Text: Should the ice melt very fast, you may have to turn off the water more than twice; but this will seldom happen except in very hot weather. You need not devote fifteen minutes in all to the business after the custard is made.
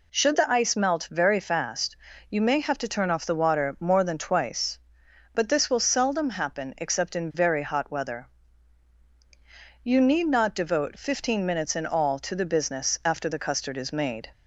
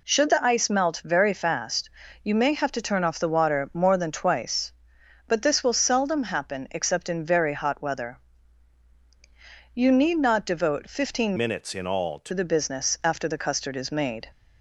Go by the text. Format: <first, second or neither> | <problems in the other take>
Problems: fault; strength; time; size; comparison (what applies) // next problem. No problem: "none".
first | changes voice from "minutes" to "to"; from 11.3 to 12.3 s; 1.0 s long